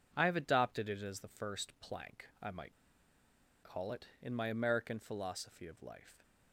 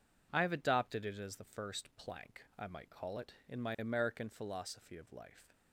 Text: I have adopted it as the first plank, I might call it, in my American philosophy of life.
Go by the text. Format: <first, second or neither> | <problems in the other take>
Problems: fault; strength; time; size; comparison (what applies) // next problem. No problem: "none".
second | pauses between "might" and "call"; noticeable; at 2.7 s; 0.90 s long